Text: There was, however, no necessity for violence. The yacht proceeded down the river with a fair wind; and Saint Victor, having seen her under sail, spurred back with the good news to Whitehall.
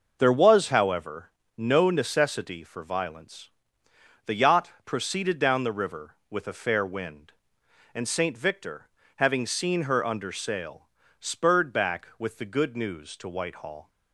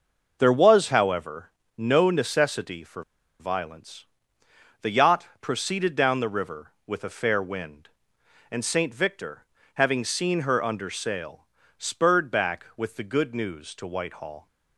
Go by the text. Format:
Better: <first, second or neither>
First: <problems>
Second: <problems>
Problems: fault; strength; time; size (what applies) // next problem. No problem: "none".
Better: first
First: none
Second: pauses between "for" and "violence"; at 3.0 s; 0.36 s long